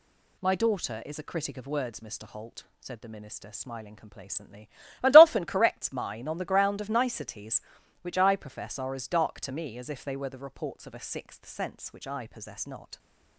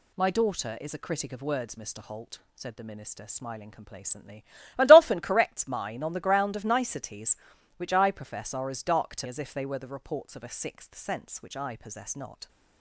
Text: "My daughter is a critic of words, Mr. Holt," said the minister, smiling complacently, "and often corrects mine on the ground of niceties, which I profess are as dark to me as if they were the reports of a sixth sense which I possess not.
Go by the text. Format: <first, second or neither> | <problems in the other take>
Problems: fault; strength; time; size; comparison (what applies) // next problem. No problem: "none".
first | skips "me"; at 9.2 s